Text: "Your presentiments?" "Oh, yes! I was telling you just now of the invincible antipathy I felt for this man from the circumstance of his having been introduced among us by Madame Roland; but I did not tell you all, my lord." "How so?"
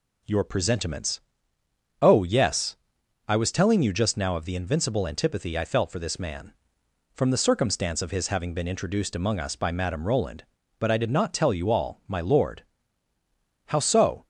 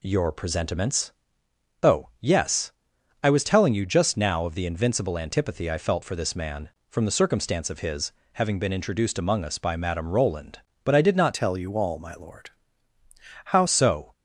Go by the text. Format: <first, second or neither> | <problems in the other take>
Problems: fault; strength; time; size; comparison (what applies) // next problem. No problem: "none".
first | pauses between "his" and "having"; slight; at 8.1 s; 0.20 s long // changes voice from "tell" to "How"; from 11.3 to 13.6 s; 2.3 s long